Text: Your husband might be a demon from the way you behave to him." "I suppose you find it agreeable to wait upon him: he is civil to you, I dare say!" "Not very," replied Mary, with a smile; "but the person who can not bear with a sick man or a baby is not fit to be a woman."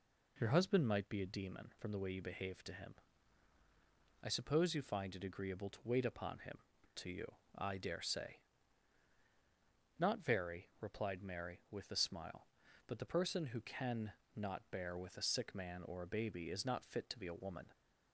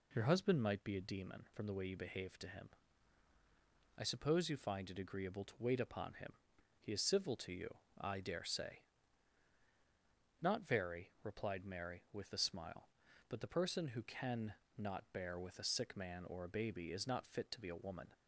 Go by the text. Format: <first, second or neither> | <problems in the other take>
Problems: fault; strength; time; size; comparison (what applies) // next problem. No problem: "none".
second | skips "he is civil"; at 6.7 s // pauses between "can" and "not"; slight; at 14.1 s; 0.22 s long; slight in the second